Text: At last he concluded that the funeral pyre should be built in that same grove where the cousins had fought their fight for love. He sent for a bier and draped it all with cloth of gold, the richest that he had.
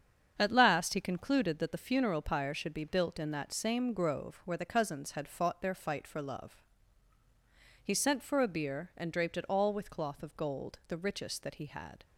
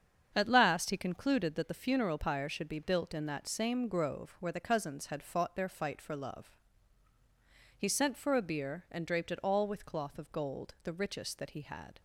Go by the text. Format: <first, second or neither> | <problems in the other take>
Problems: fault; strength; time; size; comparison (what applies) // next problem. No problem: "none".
neither | starts louder than the rest; strong; the same in both